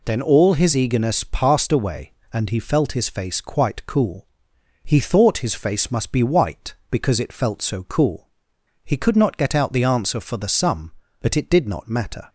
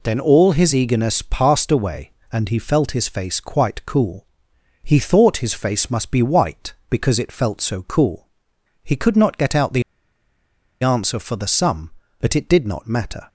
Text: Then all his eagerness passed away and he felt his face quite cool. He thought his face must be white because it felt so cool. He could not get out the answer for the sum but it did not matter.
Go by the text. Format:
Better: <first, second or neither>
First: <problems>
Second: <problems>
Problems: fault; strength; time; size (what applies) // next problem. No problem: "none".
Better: first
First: none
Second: pauses between "the" and "answer"; at 9.8 s; 0.99 s long